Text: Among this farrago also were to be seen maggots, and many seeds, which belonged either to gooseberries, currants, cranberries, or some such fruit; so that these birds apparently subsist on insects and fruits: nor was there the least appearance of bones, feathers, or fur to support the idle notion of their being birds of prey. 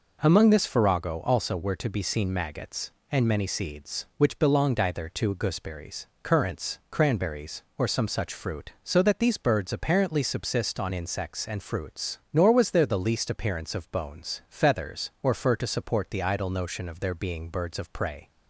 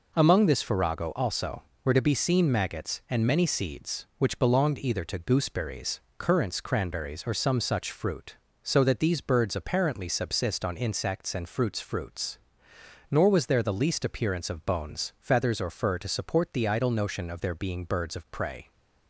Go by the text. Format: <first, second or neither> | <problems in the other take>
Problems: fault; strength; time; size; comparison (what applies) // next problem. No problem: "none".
first | says "fruits" twice; at 11.8 s